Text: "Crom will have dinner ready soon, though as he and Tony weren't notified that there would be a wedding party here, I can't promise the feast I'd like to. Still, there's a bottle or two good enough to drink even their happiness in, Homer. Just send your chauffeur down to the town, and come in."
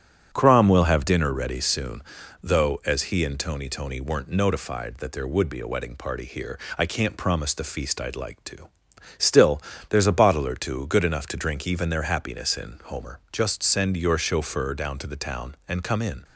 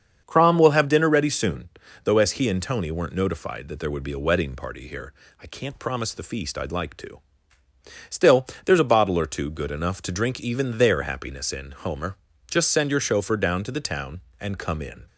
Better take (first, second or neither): second